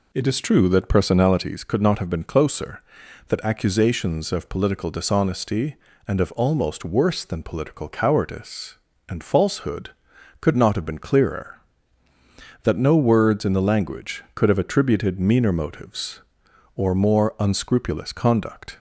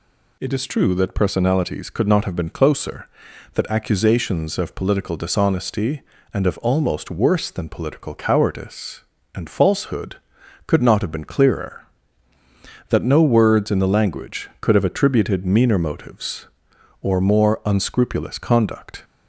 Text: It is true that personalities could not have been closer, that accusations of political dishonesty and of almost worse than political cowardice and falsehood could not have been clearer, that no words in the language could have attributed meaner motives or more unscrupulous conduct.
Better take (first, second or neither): second